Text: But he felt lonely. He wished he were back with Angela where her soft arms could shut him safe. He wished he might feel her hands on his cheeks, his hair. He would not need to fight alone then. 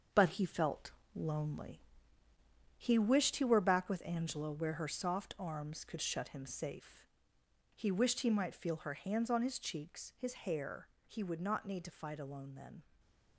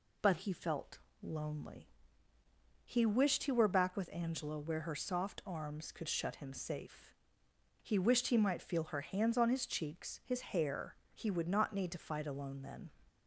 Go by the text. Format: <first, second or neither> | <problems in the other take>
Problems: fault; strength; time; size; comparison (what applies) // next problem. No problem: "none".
second | gets quieter; strong; throughout; 7.5 dB // pauses between "felt" and "lonely"; slight; at 0.9 s; 0.24 s long; slight in the second // stays silent after the last word; slight; from 12.8 s on; 0.5 s long